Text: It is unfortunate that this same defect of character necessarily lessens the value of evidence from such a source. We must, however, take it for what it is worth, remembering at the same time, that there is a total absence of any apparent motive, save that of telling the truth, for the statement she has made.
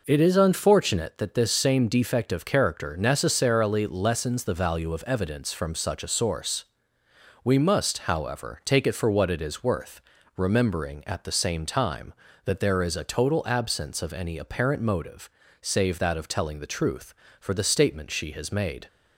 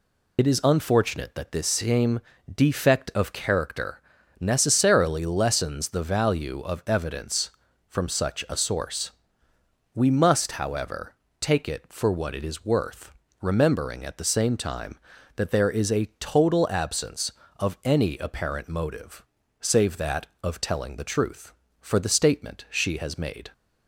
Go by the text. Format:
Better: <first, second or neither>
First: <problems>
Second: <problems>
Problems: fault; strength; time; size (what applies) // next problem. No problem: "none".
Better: first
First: none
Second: loses the start of "It"; at 0.3 s; 55 ms // pauses between "same" and "defect"; slight; at 2.1 s; 0.34 s long // pauses between "character" and "necessarily"; at 4.0 s; 0.38 s long